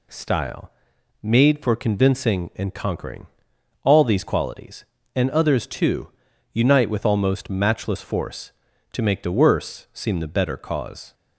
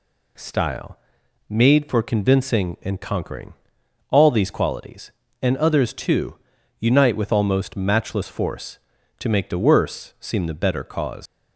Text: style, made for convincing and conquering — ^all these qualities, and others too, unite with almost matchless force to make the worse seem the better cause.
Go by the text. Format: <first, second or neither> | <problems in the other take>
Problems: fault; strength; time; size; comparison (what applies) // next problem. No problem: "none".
first | leaves "cause" unfinished; at 11.2 s; 145 ms